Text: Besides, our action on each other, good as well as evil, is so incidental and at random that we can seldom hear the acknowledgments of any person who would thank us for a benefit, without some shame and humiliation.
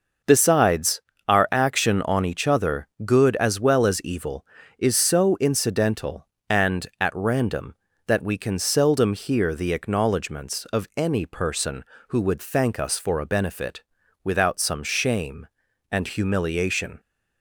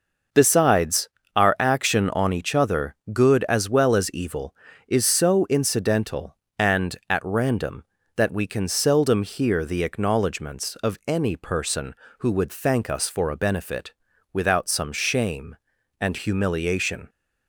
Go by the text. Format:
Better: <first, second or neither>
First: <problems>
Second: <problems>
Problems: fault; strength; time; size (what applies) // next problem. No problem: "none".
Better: neither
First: none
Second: none